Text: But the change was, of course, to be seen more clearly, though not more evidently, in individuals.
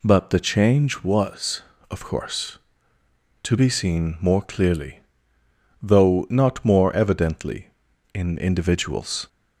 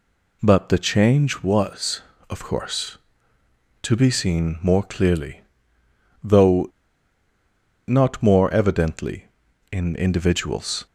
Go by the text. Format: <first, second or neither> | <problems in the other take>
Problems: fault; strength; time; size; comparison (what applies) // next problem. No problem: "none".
first | pauses between "though" and "not"; at 6.6 s; 1.2 s long